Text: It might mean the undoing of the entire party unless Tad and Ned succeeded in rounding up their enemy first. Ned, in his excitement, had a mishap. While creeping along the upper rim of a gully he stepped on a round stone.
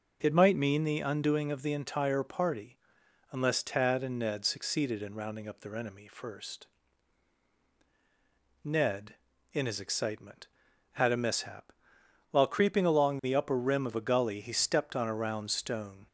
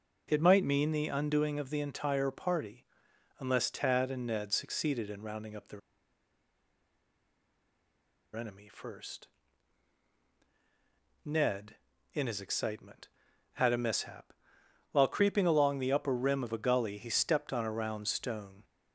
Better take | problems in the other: first | pauses between "party" and "unless"; noticeable; at 2.8 s; 0.54 s long; noticeable in the first // pauses between "their" and "enemy"; strong; at 5.8 s; 2.5 s long

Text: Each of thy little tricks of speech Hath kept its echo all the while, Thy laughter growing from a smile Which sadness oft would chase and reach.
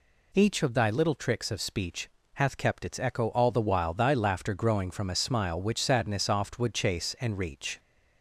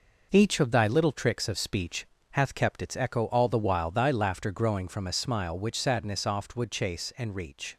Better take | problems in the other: first | gets quieter; noticeable; throughout; 6 dB // pauses between "speech" and "Hath"; slight; at 2.0 s; 0.26 s long; slight in the first

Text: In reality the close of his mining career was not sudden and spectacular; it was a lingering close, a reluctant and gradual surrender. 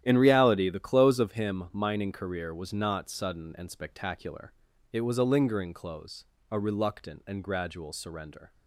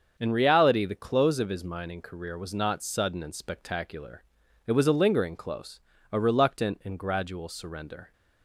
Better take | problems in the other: second | starts louder than the rest; strong; until 1.0 s; 11 dB; also in the second // says "him" for "his"; at 1.3 s

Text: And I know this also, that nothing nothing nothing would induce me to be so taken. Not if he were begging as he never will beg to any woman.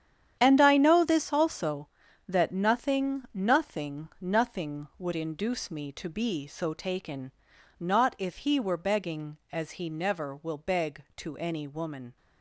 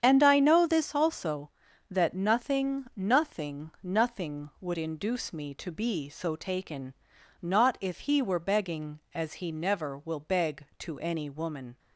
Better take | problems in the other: second | gets quieter; strong; throughout; 11.5 dB // starts louder than the rest; strong; until 1.4 s; 9.5 dB; strong in the second

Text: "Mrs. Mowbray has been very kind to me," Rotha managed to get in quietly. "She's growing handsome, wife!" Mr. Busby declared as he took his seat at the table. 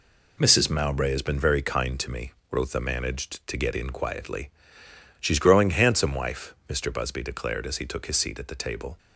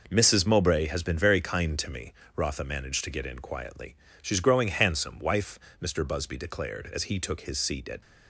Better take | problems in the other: first | stops before "the table"; at 8.0 s

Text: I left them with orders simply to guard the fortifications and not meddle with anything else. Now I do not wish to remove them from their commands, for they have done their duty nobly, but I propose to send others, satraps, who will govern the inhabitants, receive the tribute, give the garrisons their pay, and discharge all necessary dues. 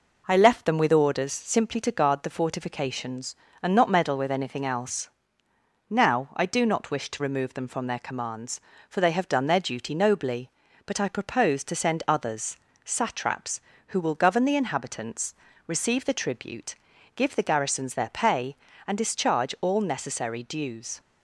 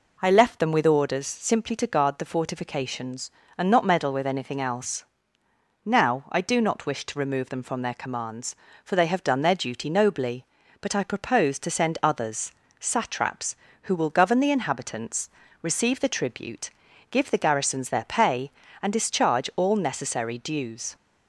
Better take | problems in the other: second | gets quieter; slight; throughout; 2.5 dB

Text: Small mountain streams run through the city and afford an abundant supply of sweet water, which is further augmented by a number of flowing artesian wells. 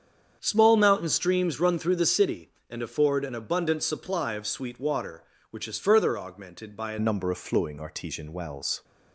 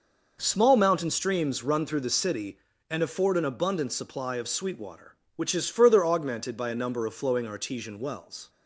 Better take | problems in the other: second | starts louder than the rest; strong; until 1.4 s; 8 dB // changes voice at "number"; from 6.9 s on; 1.9 s long

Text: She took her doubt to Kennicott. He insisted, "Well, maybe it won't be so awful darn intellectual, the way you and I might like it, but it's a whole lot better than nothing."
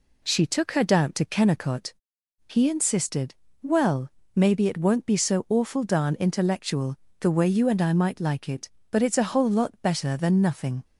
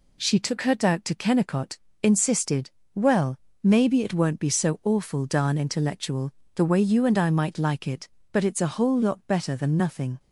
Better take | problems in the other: first | skips "He"; at 1.8 s

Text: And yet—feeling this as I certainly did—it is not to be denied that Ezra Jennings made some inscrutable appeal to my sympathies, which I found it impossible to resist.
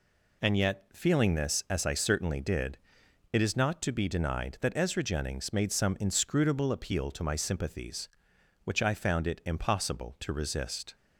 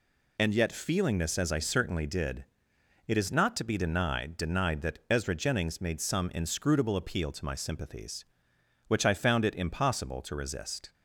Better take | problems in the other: first | says "denied" twice; at 4.3 s

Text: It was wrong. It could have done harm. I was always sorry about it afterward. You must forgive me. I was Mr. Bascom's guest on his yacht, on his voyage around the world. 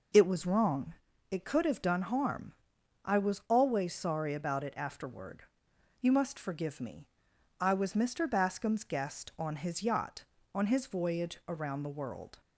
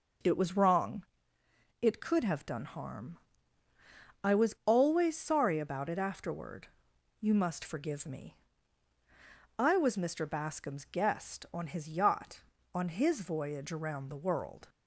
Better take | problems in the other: neither | none

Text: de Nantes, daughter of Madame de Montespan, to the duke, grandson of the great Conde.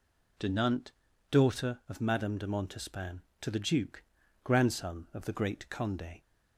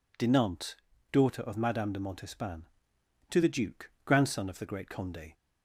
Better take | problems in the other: neither | none

